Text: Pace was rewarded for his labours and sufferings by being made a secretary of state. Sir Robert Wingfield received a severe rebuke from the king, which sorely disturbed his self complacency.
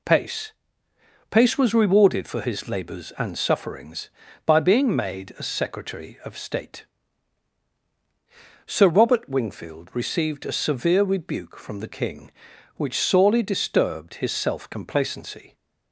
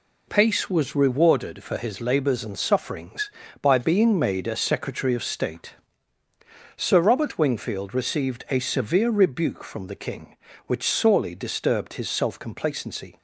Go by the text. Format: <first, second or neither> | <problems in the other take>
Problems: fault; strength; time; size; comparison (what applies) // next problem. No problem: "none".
second | says "Pace" twice; at 1.2 s